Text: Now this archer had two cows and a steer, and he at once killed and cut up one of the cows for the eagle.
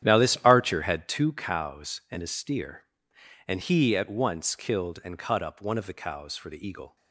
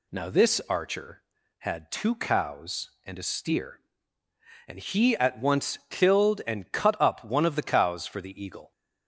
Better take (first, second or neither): second